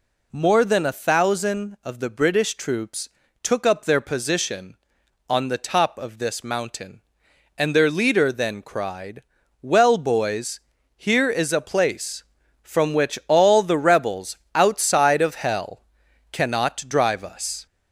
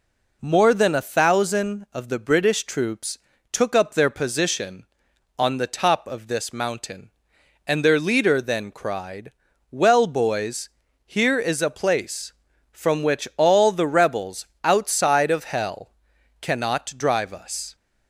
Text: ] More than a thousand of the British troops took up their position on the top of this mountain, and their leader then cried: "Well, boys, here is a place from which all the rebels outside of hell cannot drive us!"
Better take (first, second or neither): second